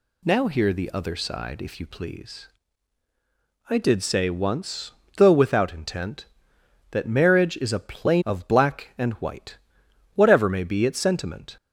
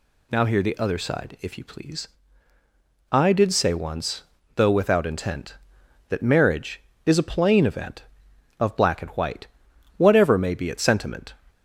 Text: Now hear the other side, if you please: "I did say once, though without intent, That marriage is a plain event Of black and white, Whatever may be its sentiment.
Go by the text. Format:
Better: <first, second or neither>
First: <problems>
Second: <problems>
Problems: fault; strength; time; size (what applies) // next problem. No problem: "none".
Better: second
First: skips "event"; at 8.2 s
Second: none